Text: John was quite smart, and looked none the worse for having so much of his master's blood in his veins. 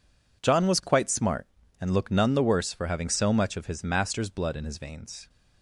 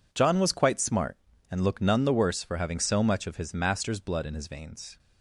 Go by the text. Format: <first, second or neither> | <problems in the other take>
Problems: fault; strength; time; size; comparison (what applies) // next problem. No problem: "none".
neither | none